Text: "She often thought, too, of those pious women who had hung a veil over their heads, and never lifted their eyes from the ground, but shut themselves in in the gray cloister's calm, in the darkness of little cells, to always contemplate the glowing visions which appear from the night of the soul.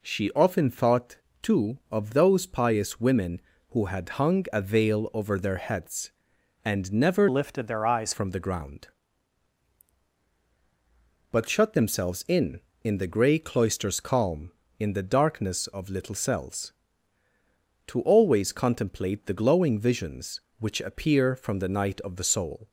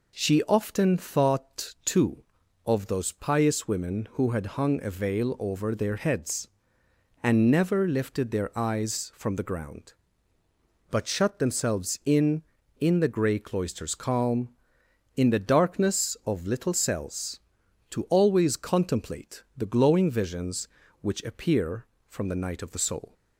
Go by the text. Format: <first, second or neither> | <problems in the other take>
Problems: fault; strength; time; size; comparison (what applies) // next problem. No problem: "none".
second | changes voice from "lifted" to "eyes"; from 7.2 to 8.1 s; 0.9 s long